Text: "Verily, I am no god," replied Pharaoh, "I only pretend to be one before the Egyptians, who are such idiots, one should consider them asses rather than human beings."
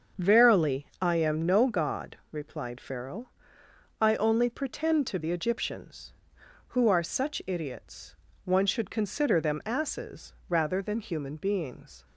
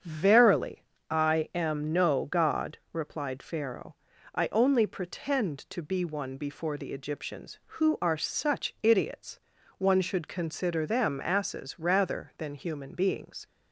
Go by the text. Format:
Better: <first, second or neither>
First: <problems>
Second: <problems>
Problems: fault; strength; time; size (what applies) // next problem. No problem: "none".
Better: second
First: starts louder than the rest; until 1.3 s; 6.5 dB // skips "be one before"; at 5.1 s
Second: starts louder than the rest; strong; until 1.3 s; 7.5 dB